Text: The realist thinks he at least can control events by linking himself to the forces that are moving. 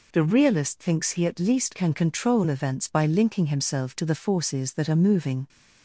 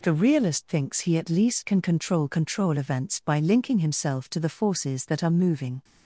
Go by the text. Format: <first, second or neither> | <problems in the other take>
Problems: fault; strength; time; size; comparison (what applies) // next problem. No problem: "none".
first | says "control" twice; at 2.2 s